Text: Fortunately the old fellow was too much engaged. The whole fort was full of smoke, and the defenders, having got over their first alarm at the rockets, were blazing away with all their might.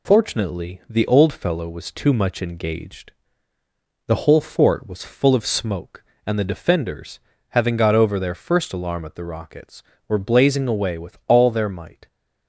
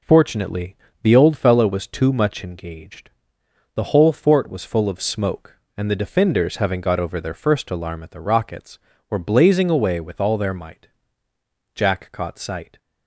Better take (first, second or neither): first